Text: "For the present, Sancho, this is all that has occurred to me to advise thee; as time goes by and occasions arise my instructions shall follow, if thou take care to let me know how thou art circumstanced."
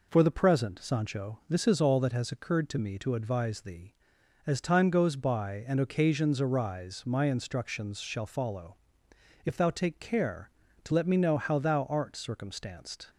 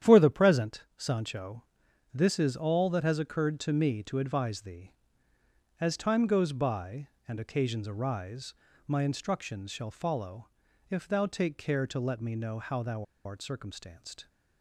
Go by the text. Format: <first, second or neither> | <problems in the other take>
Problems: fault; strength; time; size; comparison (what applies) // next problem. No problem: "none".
first | starts louder than the rest; strong; until 1.1 s; 10 dB // pauses between "arise" and "my"; slight; at 8.5 s; 0.32 s long // pauses between "thou" and "art"; slight; at 13.0 s; 0.20 s long